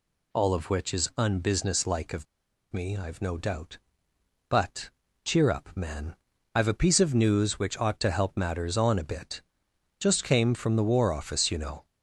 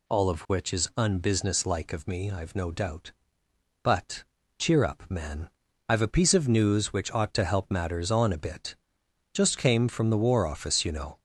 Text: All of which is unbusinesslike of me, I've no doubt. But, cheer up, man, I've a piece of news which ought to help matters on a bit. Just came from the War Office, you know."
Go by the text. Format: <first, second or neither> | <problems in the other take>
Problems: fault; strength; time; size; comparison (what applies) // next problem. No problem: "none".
second | pauses between "of" and "me"; noticeable; at 2.2 s; 0.47 s long